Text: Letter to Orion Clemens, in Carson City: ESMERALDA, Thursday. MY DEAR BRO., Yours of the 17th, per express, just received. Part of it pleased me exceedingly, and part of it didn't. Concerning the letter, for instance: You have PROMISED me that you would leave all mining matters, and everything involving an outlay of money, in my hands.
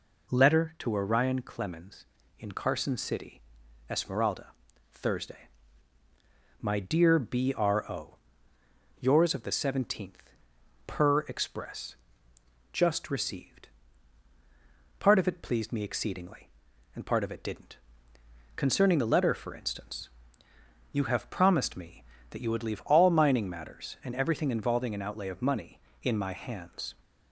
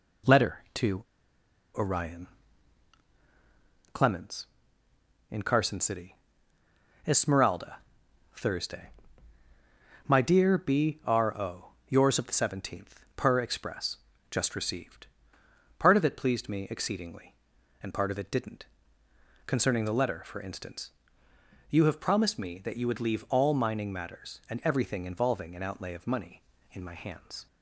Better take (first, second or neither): first